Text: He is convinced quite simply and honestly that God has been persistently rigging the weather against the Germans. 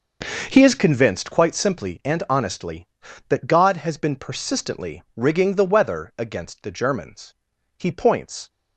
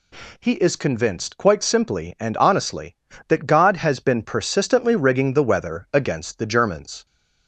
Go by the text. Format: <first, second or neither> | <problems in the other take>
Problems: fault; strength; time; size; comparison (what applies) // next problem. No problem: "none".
second | goes on to say "He points"; noticeable; from 7.7 s on; 0.74 s long